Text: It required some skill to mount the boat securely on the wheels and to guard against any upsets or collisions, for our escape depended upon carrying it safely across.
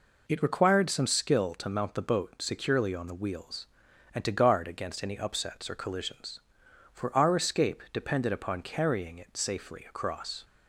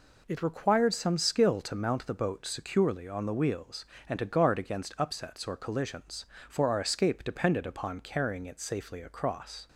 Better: first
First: none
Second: skips "any"; at 4.9 s

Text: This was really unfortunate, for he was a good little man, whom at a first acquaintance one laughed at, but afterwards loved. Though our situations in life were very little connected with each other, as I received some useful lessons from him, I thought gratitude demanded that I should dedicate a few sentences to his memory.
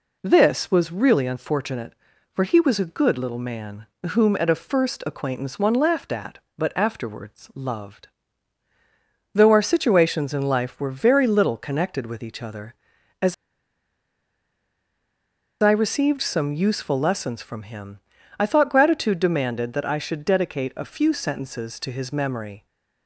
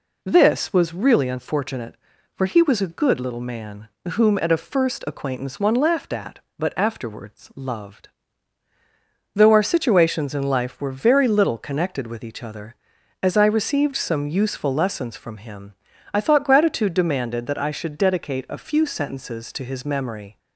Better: second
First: pauses between "as" and "I"; strong; at 13.3 s; 2.2 s long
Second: none

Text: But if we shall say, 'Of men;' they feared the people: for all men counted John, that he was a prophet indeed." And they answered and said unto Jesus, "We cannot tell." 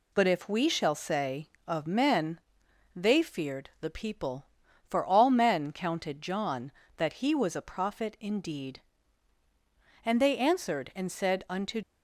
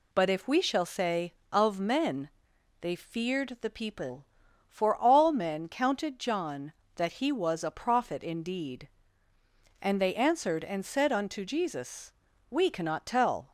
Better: second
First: stops before "Jesus We cannot tell"; at 11.8 s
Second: none

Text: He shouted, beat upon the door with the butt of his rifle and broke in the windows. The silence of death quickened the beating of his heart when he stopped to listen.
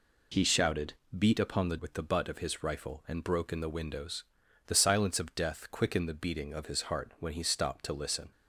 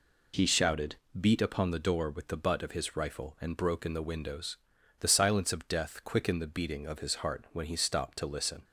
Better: second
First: skips "door"; at 1.7 s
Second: none

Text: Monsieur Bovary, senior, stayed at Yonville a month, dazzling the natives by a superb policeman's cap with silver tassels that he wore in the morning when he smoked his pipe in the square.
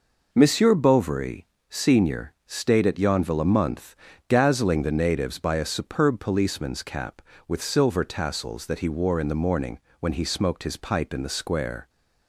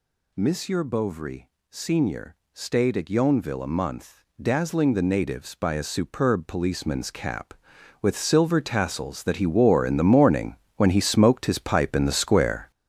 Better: first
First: pauses between "morning" and "when"; slight; at 9.7 s; 0.22 s long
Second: gets louder; strong; throughout; 8.5 dB // pauses between "morning" and "when"; slight; at 10.5 s; 0.22 s long

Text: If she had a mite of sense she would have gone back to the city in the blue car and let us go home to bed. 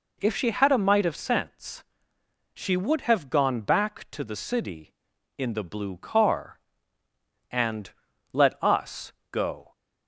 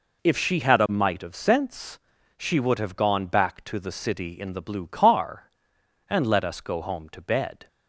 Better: second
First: pauses between "sense" and "she"; noticeable; at 1.8 s; 0.72 s long // pauses between "and" and "let"; at 7.9 s; 0.40 s long // pauses between "us" and "go"; slight; at 9.1 s; 0.22 s long // stops before "home to bed"; at 9.7 s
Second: pauses between "sense" and "she"; at 1.9 s; 0.40 s long

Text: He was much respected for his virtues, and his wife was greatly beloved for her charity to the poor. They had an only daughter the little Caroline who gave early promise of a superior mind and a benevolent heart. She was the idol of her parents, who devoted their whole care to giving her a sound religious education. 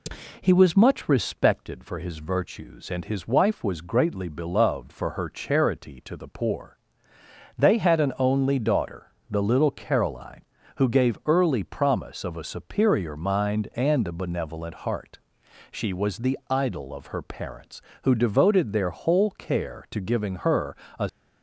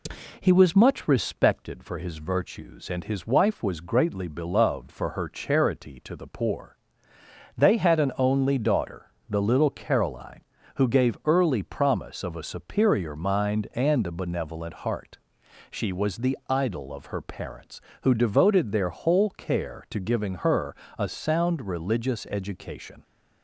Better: second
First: pauses between "daughter" and "the"; slight; at 9.0 s; 0.26 s long // pauses between "her" and "a"; slight; at 20.7 s; 0.20 s long // stops before "sound religious education"; at 21.0 s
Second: pauses between "daughter" and "the"; slight; at 9.0 s; 0.26 s long // pauses between "her" and "a"; slight; at 20.7 s; 0.20 s long

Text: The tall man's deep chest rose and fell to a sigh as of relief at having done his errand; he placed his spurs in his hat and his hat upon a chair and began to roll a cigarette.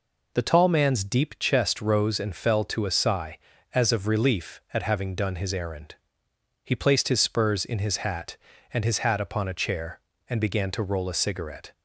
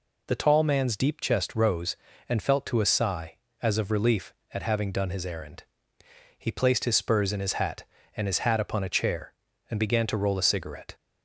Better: first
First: none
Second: says "felt" for "fell"; at 2.4 s

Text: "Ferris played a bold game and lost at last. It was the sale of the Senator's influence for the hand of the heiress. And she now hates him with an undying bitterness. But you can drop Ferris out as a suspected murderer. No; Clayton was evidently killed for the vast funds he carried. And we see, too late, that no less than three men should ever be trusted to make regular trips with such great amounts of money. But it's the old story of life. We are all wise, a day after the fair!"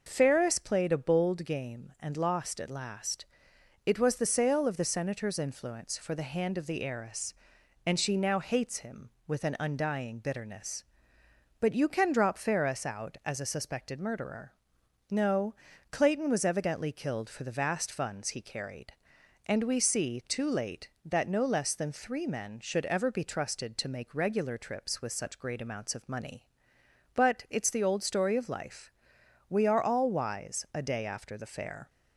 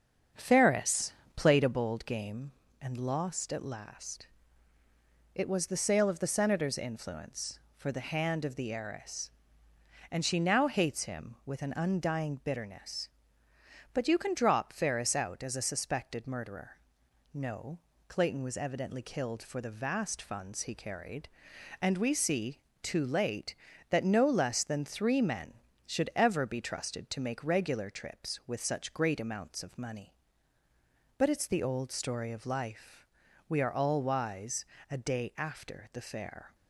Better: first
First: none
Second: starts louder than the rest; until 1.8 s; 7 dB // pauses between "Ferris" and "played"; slight; at 1.1 s; 0.24 s long

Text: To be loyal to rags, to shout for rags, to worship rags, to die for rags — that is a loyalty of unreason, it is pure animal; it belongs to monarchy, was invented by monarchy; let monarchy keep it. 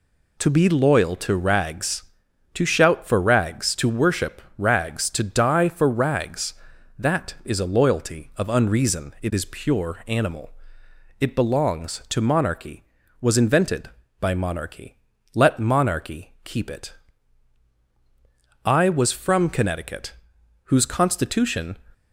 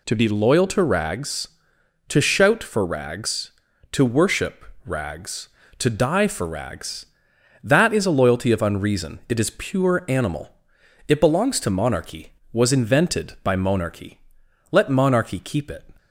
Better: second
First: pauses between "worship" and "rags"; slight; at 4.4 s; 0.16 s long // goes on to say "I was from Connecticut whose Constitution"; strong; from 18.6 s on; 3.1 s long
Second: pauses between "worship" and "rags"; slight; at 4.6 s; 0.20 s long

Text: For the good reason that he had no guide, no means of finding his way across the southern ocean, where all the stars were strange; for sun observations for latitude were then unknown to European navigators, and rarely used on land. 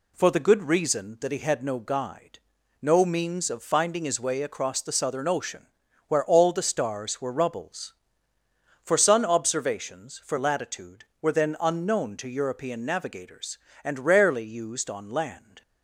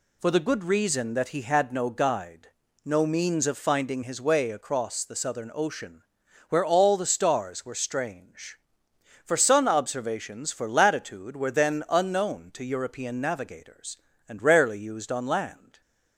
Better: second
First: says "rubbles" for "strange"; at 7.3 s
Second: none

